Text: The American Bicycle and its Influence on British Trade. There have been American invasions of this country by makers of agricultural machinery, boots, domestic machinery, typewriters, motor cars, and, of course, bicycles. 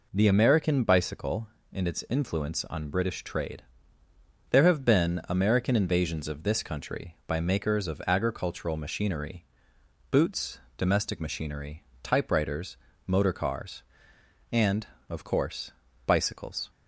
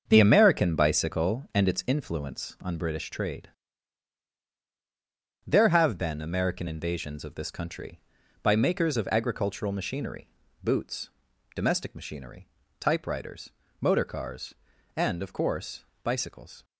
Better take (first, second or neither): first